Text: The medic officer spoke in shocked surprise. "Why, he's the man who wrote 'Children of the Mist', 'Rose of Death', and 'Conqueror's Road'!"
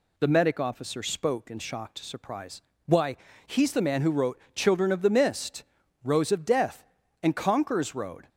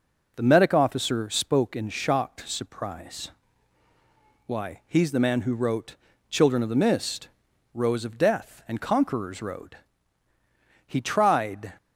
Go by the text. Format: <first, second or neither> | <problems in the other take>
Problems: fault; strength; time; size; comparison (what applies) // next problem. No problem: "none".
first | pauses between "wrote" and "Children"; slight; at 5.9 s; 0.34 s long; slight in the first // goes on to say "He tried"; noticeable; from 10.8 s on; 0.86 s long